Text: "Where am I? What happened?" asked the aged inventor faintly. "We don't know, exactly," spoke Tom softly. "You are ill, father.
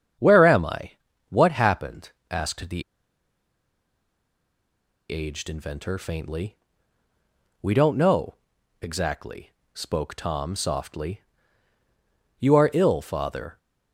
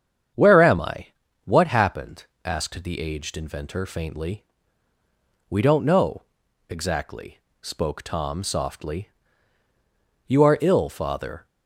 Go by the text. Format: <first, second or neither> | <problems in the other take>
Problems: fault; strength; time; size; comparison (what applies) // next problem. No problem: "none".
second | starts louder than the rest; strong; until 1.5 s; 8 dB; strong in the second // pauses between "the" and "aged"; strong; at 2.8 s; 2.2 s long